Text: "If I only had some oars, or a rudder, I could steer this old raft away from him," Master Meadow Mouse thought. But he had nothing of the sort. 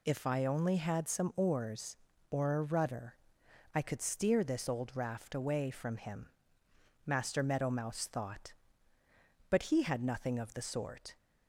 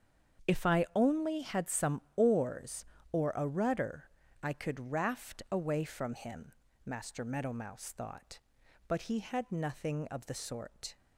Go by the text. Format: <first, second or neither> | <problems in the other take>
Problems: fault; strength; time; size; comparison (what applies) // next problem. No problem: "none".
first | starts louder than the rest; strong; until 1.5 s; 7.5 dB // pauses between "some" and "oars"; slight; at 2.0 s; 0.16 s long // skips "steer this old"; at 4.9 s